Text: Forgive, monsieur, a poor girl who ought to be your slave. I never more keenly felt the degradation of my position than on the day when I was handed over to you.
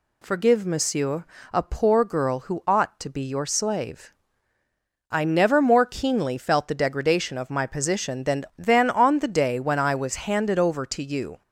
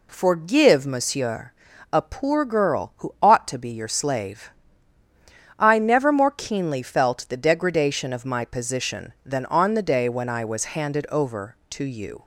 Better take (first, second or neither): second